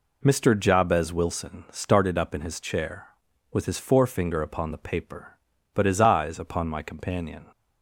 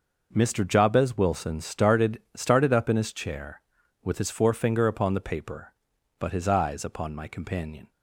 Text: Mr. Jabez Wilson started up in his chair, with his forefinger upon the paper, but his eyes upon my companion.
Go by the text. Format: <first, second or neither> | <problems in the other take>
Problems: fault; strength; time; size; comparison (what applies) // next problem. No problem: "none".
first | says "started" twice; at 2.3 s